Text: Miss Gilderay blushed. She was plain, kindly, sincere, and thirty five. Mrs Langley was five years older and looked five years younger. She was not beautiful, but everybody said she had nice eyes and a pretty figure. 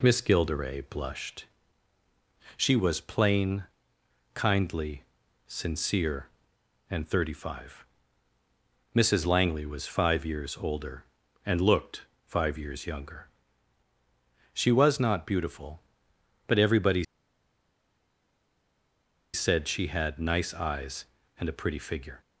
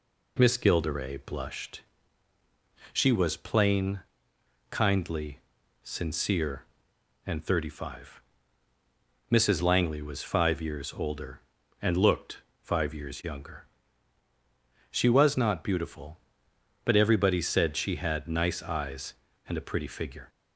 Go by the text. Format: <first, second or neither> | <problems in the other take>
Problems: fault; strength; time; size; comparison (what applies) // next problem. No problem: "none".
second | pauses between "looked" and "five"; slight; at 12.0 s; 0.24 s long; slight in the second // pauses between "everybody" and "said"; strong; at 17.0 s; 2.3 s long